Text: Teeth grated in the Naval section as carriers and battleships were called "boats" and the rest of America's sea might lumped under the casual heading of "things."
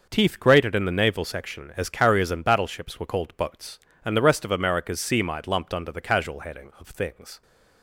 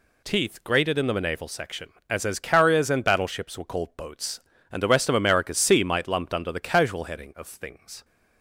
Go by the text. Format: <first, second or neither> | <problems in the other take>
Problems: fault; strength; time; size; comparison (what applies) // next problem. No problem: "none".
first | says "as" twice; at 2.2 s